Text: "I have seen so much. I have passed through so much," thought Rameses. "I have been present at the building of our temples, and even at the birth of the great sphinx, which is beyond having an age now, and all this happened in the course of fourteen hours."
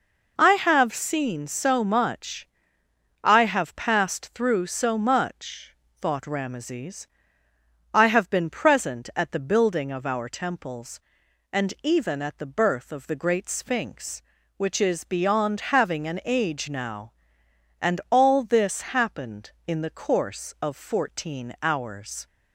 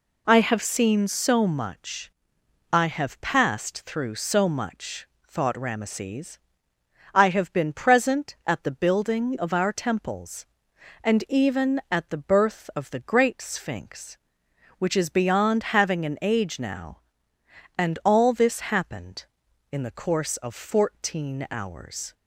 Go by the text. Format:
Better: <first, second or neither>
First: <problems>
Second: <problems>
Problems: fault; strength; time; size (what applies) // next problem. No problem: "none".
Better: neither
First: none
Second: none